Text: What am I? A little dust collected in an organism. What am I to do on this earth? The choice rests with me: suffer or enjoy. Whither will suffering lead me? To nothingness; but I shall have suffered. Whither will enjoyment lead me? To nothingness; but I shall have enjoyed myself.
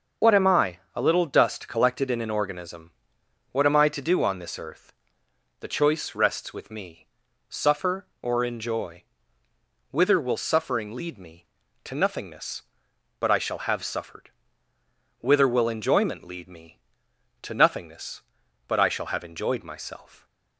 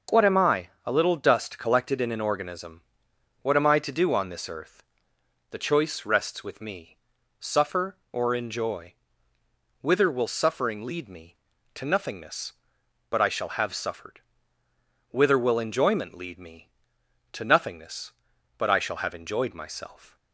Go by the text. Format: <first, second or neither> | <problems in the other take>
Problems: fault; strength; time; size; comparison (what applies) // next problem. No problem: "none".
second | loses the start of "What"; at 0.2 s; 40 ms // starts louder than the rest; until 1.4 s; 6 dB